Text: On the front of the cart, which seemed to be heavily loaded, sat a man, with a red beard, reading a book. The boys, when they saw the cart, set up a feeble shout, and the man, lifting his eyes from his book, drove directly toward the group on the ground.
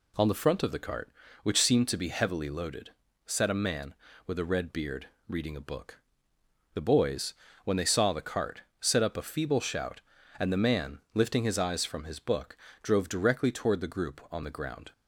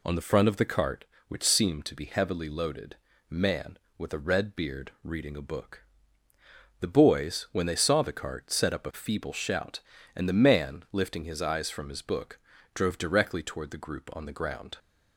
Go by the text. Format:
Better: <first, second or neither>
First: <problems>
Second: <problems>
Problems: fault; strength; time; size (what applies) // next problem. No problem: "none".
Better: first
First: none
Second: skips "sat a"; at 3.1 s